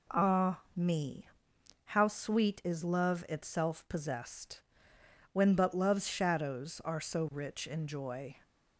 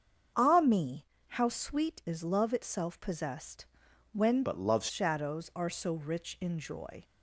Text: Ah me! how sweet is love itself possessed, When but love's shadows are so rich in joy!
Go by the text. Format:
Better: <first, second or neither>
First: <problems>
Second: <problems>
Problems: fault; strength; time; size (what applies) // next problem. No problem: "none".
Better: first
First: none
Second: starts louder than the rest; until 1.5 s; 7 dB // changes voice from "but" to "love's"; from 4.4 to 4.8 s; 0.4 s long